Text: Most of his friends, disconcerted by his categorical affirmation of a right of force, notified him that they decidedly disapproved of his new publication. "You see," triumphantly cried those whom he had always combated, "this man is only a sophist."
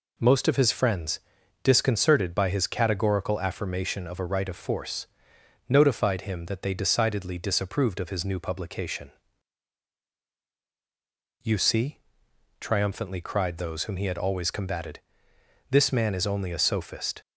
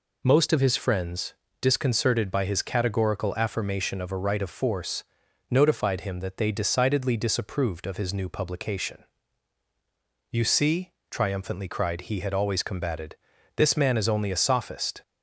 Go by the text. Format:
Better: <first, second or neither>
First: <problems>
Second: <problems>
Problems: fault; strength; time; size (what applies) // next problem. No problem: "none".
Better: first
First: none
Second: skips "those whom"; at 12.0 s